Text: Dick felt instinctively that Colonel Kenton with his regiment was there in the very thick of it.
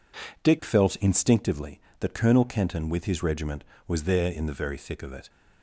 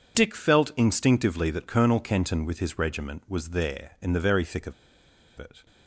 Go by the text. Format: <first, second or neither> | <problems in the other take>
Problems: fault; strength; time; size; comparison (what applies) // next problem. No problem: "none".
first | pauses between "of" and "it"; noticeable; at 4.7 s; 0.63 s long